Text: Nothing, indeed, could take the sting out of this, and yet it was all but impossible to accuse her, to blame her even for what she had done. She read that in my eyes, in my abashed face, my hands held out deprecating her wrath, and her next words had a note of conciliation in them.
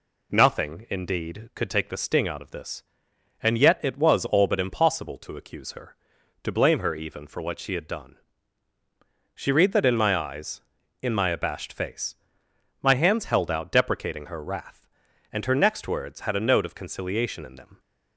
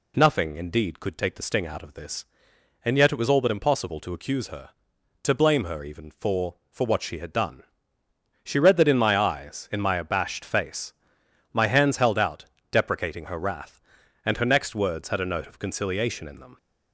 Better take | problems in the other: first | says "for" twice; at 6.7 s // pauses between "out" and "deprecating"; slight; at 12.4 s; 0.26 s long

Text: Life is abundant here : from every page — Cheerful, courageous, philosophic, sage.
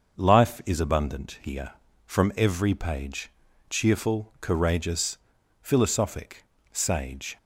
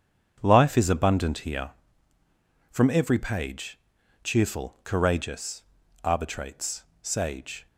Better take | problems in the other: first | starts louder than the rest; strong; until 1.4 s; 7.5 dB; also in the first // says "arbitrates" for "philosophic"; at 6.0 s

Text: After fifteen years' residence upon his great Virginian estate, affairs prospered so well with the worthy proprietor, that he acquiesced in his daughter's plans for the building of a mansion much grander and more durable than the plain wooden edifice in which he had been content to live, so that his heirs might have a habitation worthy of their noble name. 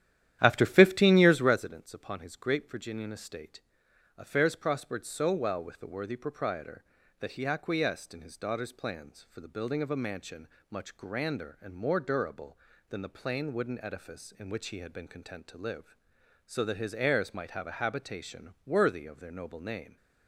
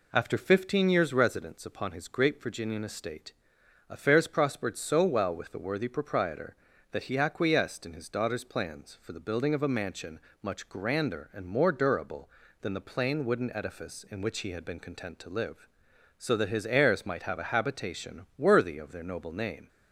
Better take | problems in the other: second | starts louder than the rest; strong; until 1.7 s; 11.5 dB // pauses between "mansion" and "much"; slight; at 10.4 s; 0.22 s long; slight in the second

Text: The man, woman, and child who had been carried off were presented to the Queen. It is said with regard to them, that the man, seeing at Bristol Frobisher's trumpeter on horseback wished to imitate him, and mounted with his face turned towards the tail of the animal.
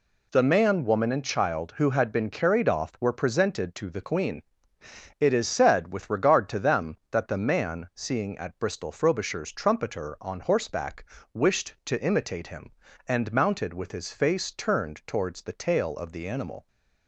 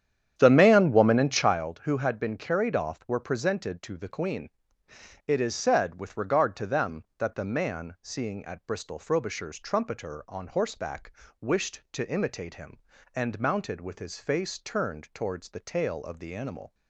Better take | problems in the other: first | starts louder than the rest; strong; until 1.7 s; 10 dB // pauses between "horseback" and "wished"; slight; at 11.1 s; 0.30 s long; slight in the first

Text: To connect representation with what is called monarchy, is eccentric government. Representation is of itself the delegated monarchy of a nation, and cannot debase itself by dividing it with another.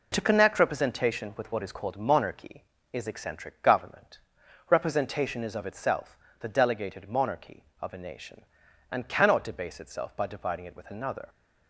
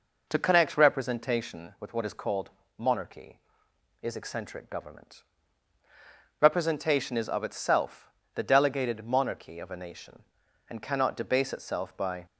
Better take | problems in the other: first | pauses between "called" and "monarchy"; slight; at 2.4 s; 0.30 s long // pauses between "itself" and "the"; slight; at 8.0 s; 0.24 s long; slight in the first // stops before "dividing it with another"; at 12.2 s

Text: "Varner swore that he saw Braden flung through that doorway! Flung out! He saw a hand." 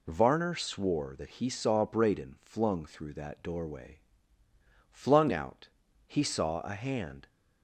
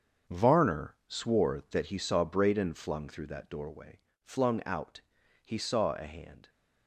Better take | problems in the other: first | gets quieter; strong; throughout; 10.5 dB

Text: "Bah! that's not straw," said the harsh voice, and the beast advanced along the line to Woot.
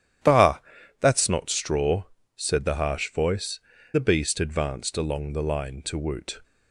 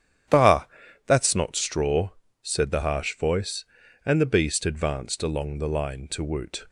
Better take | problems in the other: second | starts louder than the rest; strong; until 1.6 s; 11 dB; strong in the second // skips "and"; at 3.7 s

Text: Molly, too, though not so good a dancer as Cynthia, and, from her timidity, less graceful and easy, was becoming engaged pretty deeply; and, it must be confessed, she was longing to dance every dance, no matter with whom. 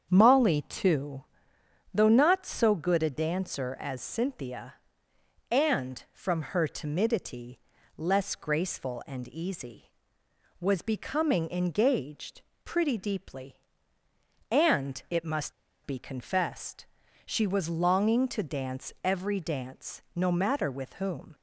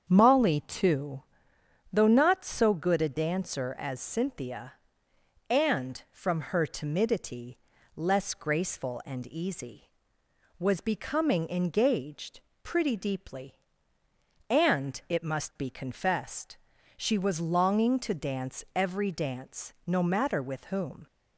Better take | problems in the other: second | starts louder than the rest; strong; until 1.1 s; 7.5 dB; strong in the second // pauses between "engaged" and "pretty"; slight; at 12.4 s; 0.24 s long; slight in the second // pauses between "must" and "be"; slight; at 15.5 s; 0.32 s long

